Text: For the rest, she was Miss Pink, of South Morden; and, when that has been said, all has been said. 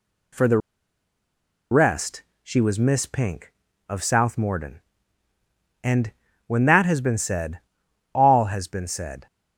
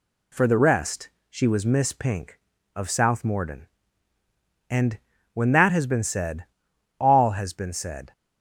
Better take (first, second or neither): second